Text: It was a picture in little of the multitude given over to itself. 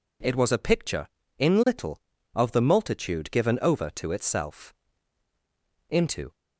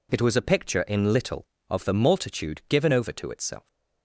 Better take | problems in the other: second | goes on to say "Into"; slight; from 5.8 s on; 0.44 s long

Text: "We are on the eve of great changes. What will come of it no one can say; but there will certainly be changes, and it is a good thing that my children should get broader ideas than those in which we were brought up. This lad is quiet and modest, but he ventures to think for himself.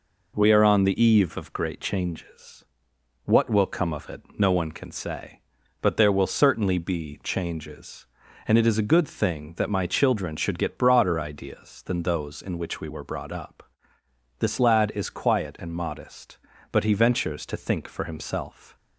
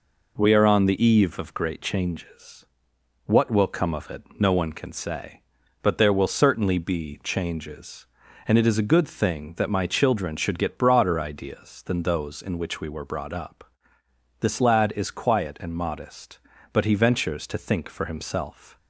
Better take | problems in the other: neither | pauses between "it" and "no"; slight; the same in both

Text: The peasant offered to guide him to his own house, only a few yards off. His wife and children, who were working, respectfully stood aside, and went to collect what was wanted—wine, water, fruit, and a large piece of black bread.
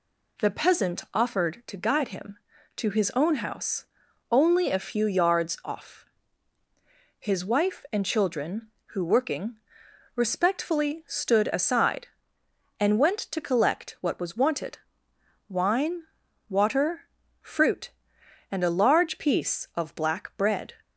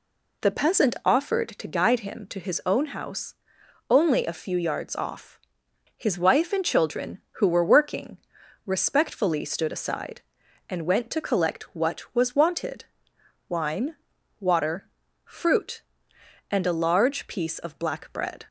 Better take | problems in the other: second | skips "were"; at 9.0 s

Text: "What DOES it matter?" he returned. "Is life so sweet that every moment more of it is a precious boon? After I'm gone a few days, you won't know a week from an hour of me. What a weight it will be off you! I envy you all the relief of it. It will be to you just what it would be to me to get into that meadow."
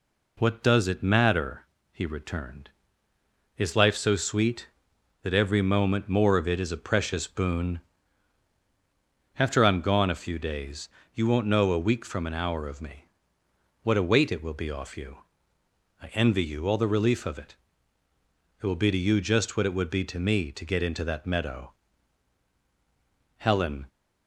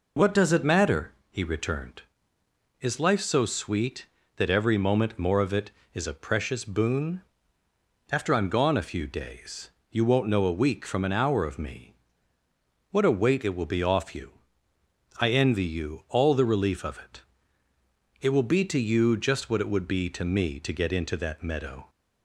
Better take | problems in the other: second | goes on to say "Helen"; from 23.3 s on; 0.50 s long

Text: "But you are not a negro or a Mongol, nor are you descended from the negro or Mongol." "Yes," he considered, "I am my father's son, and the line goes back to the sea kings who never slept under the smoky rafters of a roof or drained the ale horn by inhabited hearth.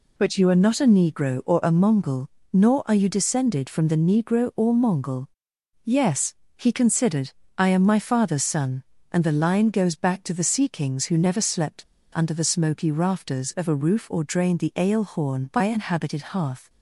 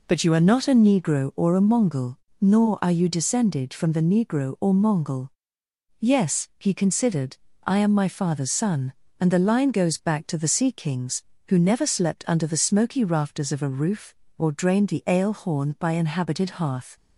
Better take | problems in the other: second | pauses between "slept" and "under"; slight; at 11.8 s; 0.31 s long

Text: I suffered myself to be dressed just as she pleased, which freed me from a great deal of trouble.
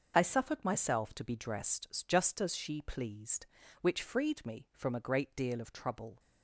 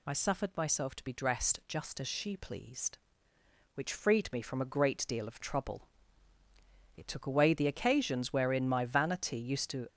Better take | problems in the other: first | goes on to say "It took away the occasions wherein my vanity used to"; strong; from 6.9 s on; 2.9 s long

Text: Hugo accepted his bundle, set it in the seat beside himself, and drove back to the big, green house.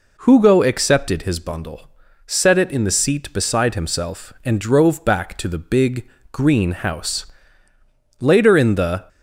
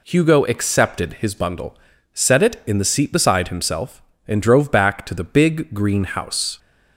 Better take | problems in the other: second | goes on to say "Later in the"; noticeable; from 8.2 s on; 0.84 s long

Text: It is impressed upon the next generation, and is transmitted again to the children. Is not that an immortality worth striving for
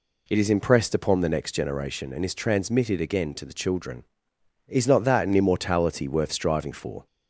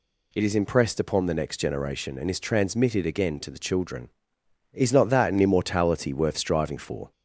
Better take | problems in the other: second | starts louder than the rest; slight; until 1.6 s; 2.5 dB

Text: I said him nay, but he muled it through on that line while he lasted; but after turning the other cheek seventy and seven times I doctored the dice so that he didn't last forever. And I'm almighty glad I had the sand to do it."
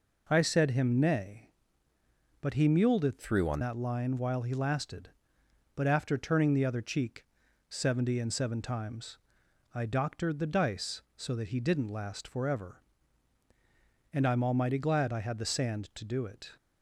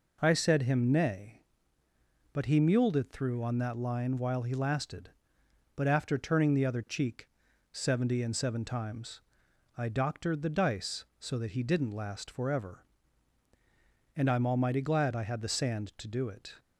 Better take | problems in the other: second | changes voice from "through" to "on"; from 3.1 to 3.5 s; 0.4 s long // pauses between "cheek" and "seventy"; noticeable; at 7.2 s; 0.46 s long; noticeable in the second // pauses between "times" and "I"; noticeable; at 9.1 s; 0.56 s long; noticeable in the second

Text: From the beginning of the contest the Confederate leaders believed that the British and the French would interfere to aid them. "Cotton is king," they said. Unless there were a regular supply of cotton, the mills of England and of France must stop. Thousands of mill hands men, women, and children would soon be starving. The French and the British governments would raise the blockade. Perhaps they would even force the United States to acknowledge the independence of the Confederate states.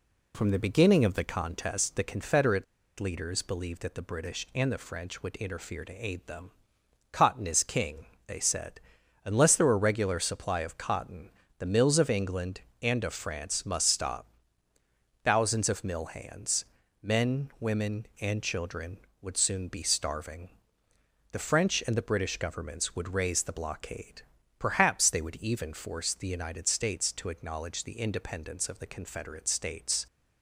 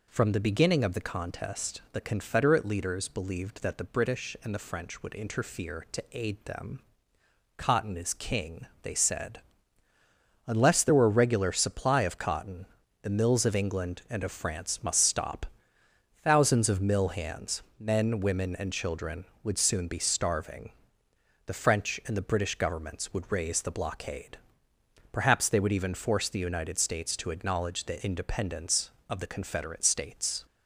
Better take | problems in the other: second | pauses between "Confederate" and "leaders"; slight; at 2.6 s; 0.35 s long // pauses between "hands" and "men"; slight; at 16.6 s; 0.34 s long; slight in the second

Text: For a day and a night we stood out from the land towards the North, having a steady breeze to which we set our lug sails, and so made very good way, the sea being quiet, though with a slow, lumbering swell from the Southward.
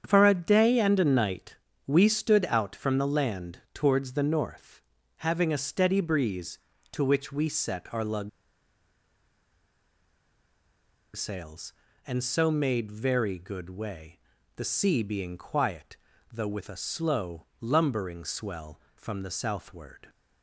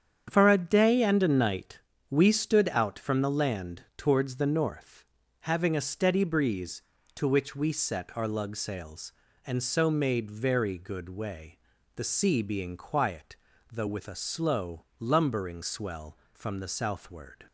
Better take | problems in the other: second | starts louder than the rest; strong; until 1.0 s; 8 dB; strong in the second // pauses between "night" and "we"; slight; at 1.5 s; 0.32 s long; slight in the second // pauses between "lug" and "sails"; strong; at 8.2 s; 2.8 s long

